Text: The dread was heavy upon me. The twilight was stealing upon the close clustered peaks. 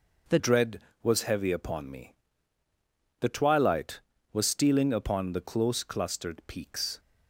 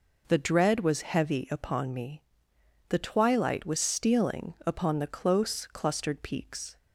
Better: second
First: changes voice at "dread"; from 0.3 s on; 6.6 s long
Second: none

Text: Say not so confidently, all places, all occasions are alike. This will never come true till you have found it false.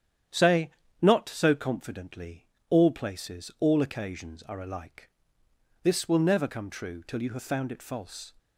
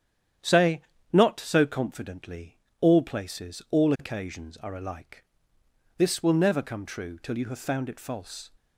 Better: neither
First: starts louder than the rest; strong; until 1.6 s; 9.5 dB // pauses between "Say" and "not"; slight; at 0.6 s; 0.30 s long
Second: starts louder than the rest; strong; until 1.7 s; 9.5 dB // pauses between "Say" and "not"; slight; at 0.8 s; 0.30 s long

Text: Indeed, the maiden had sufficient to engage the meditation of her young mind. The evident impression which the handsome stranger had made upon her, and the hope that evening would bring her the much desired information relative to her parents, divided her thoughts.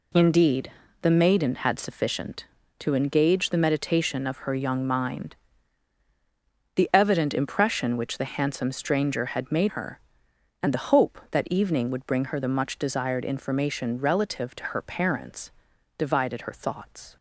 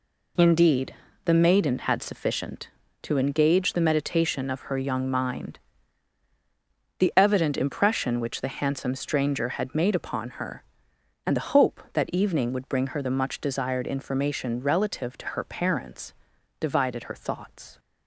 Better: second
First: skips "upon"; at 9.6 s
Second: none

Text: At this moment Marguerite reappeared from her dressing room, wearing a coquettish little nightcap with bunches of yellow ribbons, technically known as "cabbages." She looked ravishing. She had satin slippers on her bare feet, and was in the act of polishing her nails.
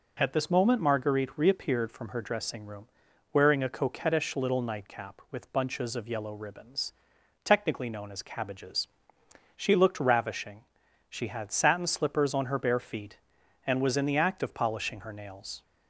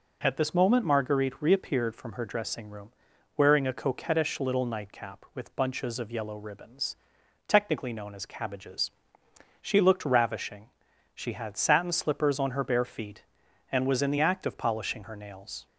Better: neither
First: none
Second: none

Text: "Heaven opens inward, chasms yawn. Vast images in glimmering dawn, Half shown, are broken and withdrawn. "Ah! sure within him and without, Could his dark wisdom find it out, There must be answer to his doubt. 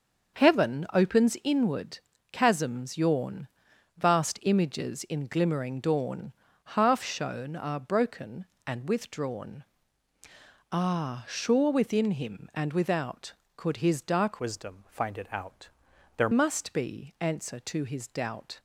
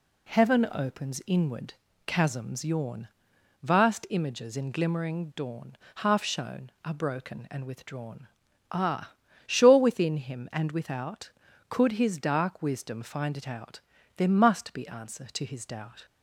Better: second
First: starts louder than the rest; until 1.5 s; 6.5 dB // changes voice from "wisdom" to "There"; from 14.4 to 16.3 s; 1.9 s long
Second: none

